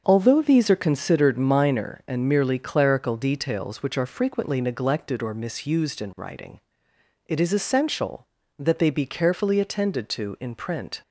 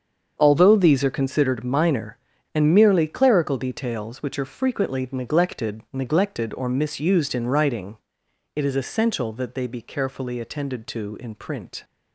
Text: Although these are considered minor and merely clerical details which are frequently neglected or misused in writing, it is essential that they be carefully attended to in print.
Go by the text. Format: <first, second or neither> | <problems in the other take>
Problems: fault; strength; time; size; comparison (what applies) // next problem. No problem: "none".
first | starts louder than the rest; until 1.3 s; 7 dB; also in the first // says "neglected" twice; at 5.9 s